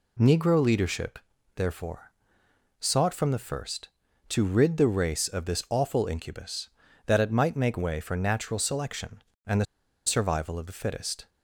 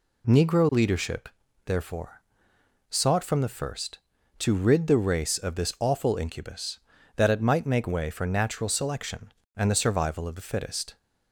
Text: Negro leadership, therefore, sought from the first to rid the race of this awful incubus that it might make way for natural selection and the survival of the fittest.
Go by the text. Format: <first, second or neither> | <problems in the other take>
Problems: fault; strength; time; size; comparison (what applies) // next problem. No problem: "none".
second | pauses between "the" and "survival"; at 9.6 s; 0.41 s long